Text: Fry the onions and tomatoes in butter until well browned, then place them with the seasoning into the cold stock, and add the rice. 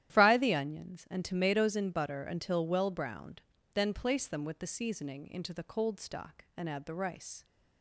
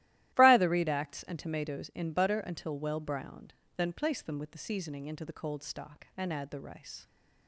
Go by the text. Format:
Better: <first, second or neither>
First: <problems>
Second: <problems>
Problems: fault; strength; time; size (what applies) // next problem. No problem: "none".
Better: first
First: starts louder than the rest; strong; until 1.1 s; 12 dB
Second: starts louder than the rest; strong; until 1.4 s; 14.5 dB // says "redacts" for "onions"; at 0.6 s